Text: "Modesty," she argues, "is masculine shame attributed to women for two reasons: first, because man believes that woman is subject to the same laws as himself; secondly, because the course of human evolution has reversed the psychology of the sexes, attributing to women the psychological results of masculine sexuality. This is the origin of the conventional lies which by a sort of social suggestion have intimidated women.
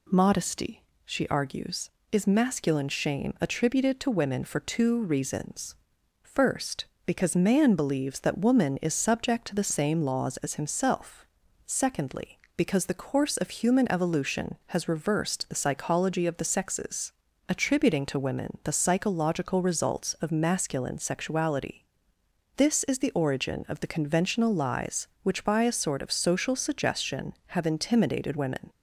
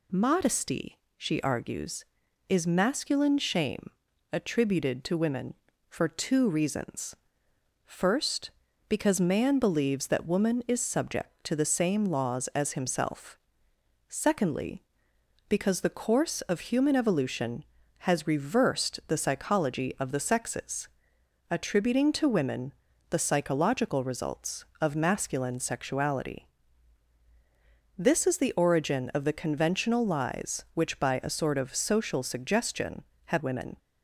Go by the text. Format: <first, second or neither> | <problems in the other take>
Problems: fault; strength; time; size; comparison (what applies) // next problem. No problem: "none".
first | pauses between "shame" and "attributed"; at 3.9 s; 0.42 s long // pauses between "women" and "the"; at 22.7 s; 0.38 s long // skips "intimidated"; at 33.4 s